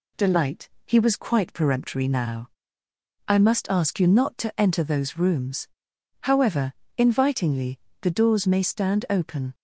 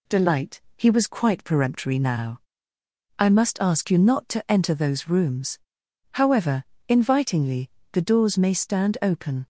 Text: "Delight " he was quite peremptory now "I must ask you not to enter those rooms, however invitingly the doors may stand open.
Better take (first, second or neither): neither